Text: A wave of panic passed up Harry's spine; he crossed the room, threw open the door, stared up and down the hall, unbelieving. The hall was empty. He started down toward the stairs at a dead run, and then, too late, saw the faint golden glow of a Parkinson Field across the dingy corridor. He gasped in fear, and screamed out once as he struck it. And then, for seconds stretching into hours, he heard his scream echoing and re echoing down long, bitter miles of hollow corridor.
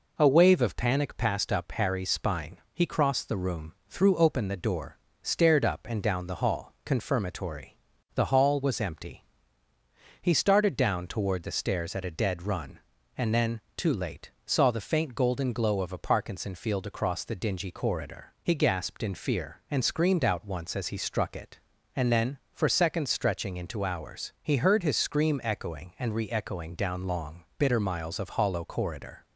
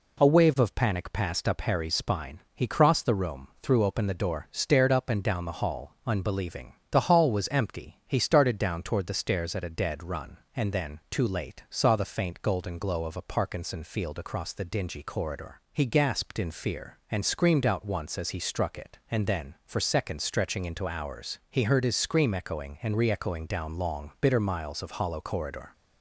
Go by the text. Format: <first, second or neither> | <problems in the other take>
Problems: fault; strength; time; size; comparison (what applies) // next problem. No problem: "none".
second | says "confirmatory" for "unbelieving"; at 6.8 s